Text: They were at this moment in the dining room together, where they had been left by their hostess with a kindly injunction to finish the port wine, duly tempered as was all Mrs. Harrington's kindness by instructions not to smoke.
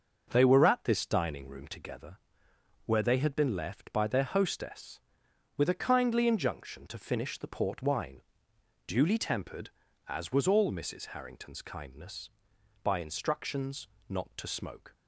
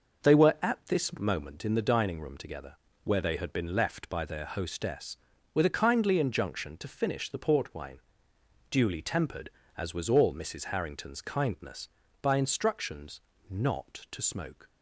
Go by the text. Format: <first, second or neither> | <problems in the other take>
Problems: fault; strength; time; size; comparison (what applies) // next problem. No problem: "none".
second | skips "moment in the"; at 1.0 s // pauses between "instructions" and "not"; slight; at 13.8 s; 0.20 s long; slight in the second